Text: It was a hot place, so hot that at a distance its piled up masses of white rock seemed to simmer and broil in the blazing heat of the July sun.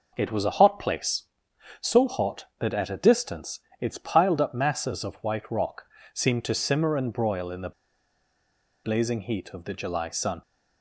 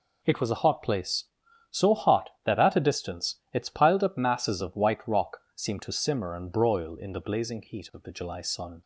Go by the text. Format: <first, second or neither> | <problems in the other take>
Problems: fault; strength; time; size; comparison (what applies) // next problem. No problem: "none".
second | pauses between "distance" and "its"; slight; at 3.6 s; 0.20 s long // pauses between "rock" and "seemed"; slight; at 5.8 s; 0.28 s long; slight in the second // pauses between "the" and "blazing"; at 7.7 s; 1.1 s long